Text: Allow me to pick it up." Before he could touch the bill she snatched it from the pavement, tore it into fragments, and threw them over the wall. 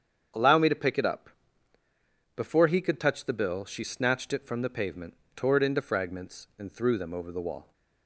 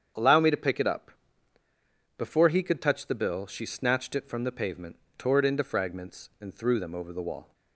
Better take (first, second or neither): neither